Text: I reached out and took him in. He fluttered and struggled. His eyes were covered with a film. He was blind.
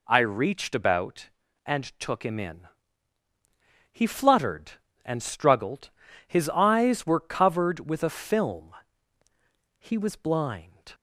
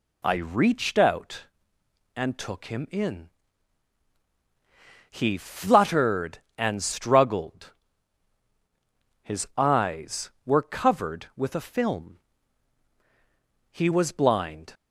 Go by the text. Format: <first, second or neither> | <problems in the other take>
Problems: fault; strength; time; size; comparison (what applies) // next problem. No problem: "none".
second | says "about" for "out"; at 0.7 s